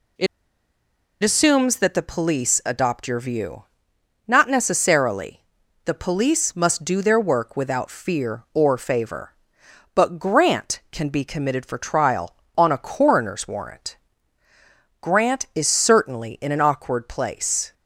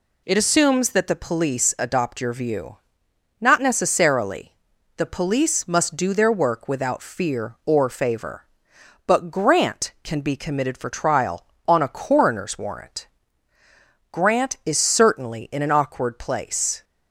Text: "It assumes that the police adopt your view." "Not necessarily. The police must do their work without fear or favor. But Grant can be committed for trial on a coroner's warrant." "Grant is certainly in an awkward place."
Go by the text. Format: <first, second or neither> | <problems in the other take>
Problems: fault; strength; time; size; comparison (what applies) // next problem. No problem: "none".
second | pauses between "It" and "assumes"; at 0.2 s; 0.98 s long